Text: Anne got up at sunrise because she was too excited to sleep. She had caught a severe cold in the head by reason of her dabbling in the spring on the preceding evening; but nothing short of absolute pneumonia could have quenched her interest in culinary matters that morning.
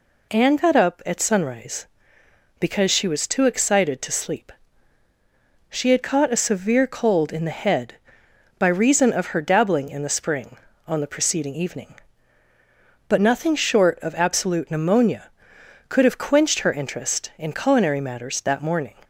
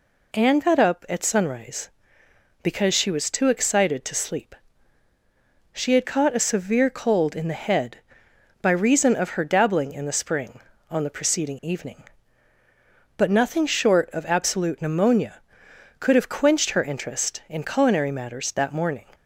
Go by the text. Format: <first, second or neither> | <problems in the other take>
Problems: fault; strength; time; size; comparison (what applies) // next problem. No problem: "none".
neither | none